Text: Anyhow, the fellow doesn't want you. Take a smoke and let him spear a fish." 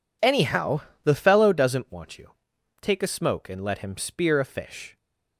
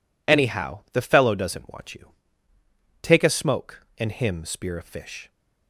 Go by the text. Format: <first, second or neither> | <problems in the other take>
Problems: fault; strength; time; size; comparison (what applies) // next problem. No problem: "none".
first | skips "let"; at 4.1 s